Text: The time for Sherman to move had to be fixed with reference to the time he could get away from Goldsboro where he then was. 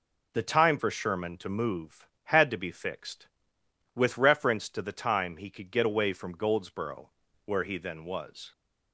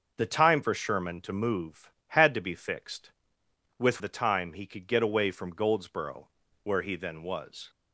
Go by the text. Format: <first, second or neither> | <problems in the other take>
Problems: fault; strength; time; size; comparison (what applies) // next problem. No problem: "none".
first | starts louder than the rest; noticeable; until 1.1 s; 6 dB // skips "reference to"; at 3.9 s // pauses between "Goldsboro" and "where"; slight; at 6.2 s; 0.36 s long; slight in the first